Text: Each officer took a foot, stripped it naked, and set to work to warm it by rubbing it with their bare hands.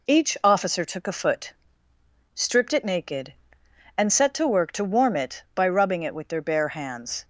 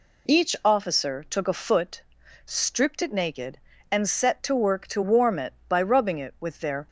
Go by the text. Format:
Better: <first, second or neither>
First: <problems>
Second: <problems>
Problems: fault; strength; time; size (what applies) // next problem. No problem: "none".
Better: first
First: none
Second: stops before "bare hands"; at 6.8 s